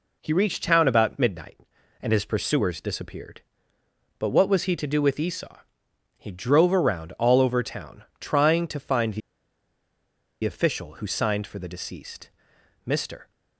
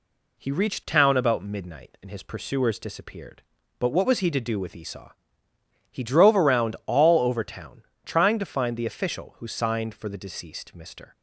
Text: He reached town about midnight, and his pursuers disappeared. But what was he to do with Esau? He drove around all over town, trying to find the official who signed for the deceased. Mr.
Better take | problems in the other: second | pauses between "the" and "official"; at 9.2 s; 1.2 s long

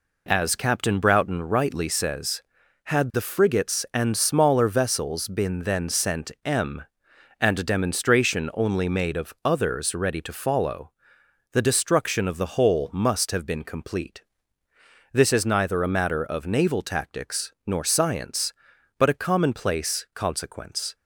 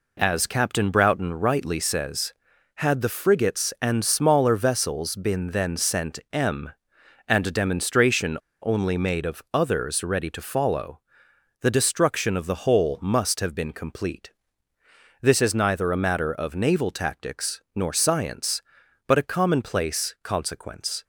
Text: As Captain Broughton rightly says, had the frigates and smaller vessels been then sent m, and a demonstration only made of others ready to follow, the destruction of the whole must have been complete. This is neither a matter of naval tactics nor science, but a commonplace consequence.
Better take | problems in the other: first | pauses between "demonstration" and "only"; slight; at 8.3 s; 0.27 s long

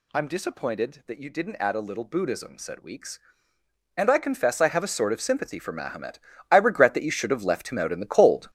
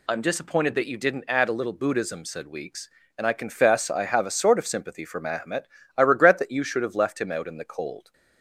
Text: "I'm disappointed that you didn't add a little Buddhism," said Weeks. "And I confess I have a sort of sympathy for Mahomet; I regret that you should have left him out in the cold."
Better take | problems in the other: second | gets louder; strong; throughout; 9.5 dB

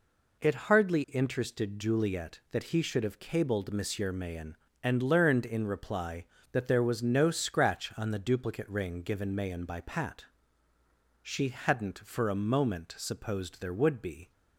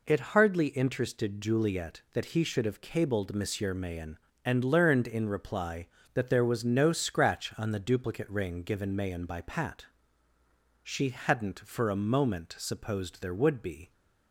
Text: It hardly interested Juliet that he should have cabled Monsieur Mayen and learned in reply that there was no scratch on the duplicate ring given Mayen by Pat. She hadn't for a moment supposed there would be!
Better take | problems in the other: neither | none

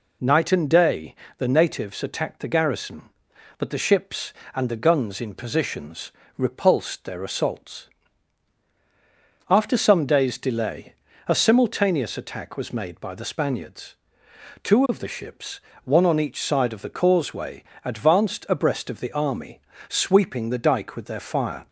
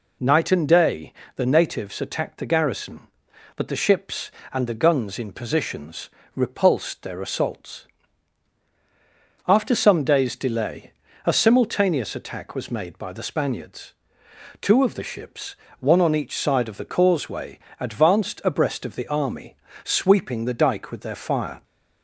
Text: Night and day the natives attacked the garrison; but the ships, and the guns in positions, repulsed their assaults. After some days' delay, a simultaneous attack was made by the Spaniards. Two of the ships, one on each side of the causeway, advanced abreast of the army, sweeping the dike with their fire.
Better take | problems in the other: neither | pauses between "day" and "the"; slight; the same in both

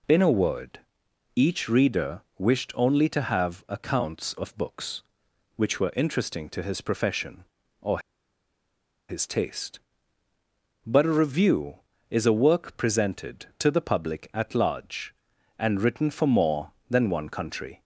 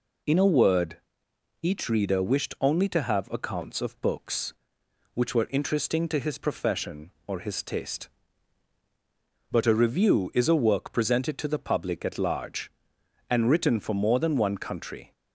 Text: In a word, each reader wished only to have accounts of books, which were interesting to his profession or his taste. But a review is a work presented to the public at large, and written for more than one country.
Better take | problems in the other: second | pauses between "reader" and "wished"; slight; at 2.2 s; 0.16 s long // pauses between "or" and "his"; at 7.9 s; 1.1 s long

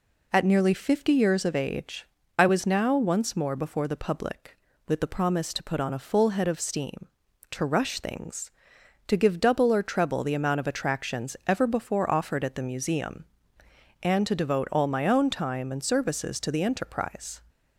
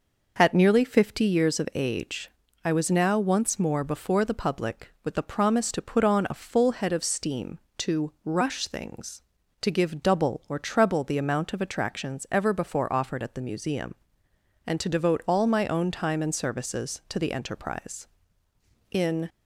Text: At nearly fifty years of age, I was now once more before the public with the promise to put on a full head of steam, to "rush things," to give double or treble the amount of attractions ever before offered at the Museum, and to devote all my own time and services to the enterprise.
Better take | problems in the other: first | goes on to say "In"; slight; from 18.9 s on; 0.38 s long

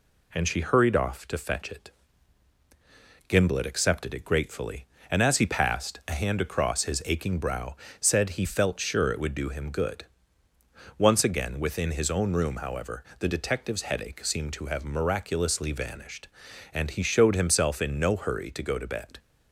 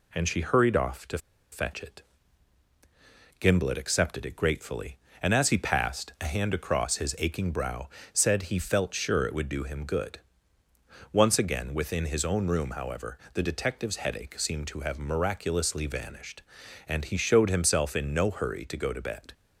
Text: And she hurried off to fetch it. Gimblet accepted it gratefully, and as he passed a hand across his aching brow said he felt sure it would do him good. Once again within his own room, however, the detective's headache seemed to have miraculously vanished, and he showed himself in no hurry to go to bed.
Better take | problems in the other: first | pauses between "to" and "fetch"; slight; at 1.1 s; 0.34 s long // pauses between "brow" and "said"; slight; at 7.8 s; 0.24 s long; slight in the first

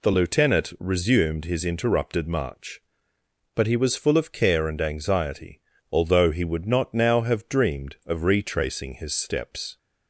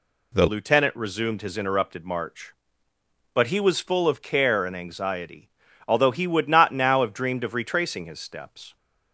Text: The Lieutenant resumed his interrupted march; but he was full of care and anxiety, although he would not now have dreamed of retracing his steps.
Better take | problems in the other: first | changes voice at "Lieutenant"; from 0.4 s on; 8.3 s long

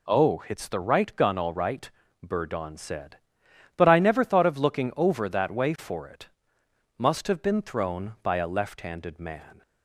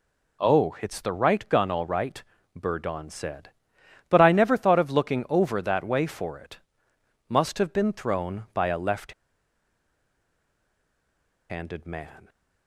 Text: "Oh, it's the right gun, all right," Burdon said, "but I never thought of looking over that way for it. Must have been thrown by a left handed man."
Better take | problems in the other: first | pauses between "left" and "handed"; strong; at 9.1 s; 2.3 s long

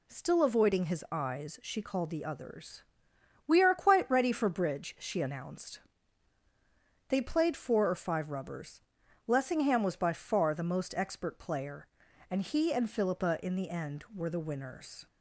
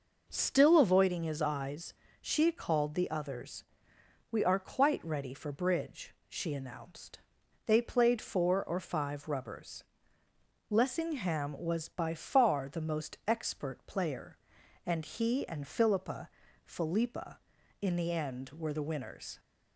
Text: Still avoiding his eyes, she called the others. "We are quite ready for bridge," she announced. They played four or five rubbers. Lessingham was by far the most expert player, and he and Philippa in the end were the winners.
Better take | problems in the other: first | says "Philippa" twice; at 16.6 s

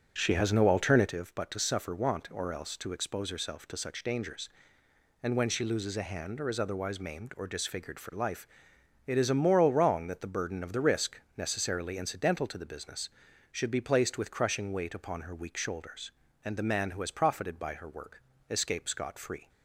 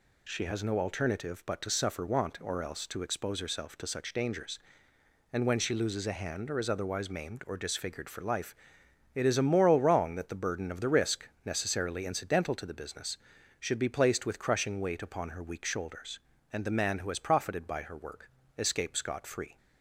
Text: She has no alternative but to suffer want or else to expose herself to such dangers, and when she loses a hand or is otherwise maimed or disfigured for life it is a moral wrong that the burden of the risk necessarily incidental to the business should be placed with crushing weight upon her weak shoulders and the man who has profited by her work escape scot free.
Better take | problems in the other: second | starts louder than the rest; noticeable; until 1.3 s; 6 dB // pauses between "life" and "it"; noticeable; at 8.4 s; 0.60 s long; noticeable in the second // pauses between "risk" and "necessarily"; slight; at 11.2 s; 0.16 s long; slight in the second // pauses between "work" and "escape"; slight; at 18.2 s; 0.30 s long; slight in the second

